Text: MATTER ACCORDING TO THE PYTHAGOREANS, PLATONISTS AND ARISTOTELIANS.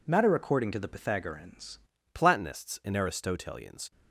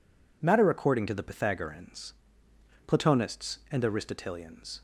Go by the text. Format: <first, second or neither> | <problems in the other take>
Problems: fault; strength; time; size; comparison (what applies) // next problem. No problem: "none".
second | changes voice at "PLATONISTS"; from 2.1 s on; 1.8 s long